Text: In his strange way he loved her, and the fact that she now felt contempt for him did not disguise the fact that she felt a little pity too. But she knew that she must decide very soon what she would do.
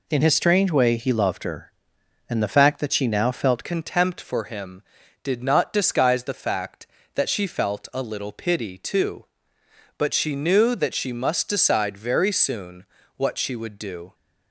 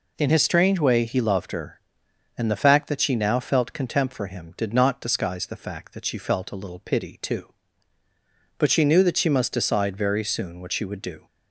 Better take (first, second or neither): second